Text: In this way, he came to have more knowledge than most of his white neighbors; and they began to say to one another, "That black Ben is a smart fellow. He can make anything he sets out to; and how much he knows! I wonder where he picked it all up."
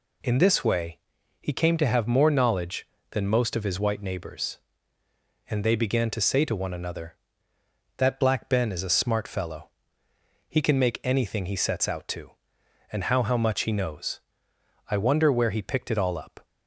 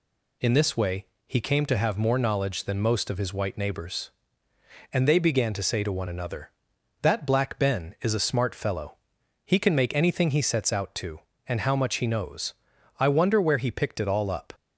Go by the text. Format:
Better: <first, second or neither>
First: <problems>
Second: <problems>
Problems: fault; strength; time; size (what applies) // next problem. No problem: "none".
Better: second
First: says "how" twice; at 13.2 s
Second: none